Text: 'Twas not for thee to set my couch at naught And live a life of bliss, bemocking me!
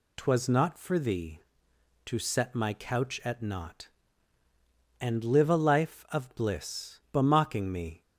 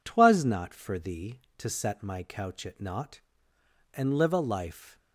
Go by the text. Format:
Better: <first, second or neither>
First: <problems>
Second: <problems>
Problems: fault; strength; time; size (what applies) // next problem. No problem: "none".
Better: first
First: none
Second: stops before "of bliss bemocking me"; at 4.9 s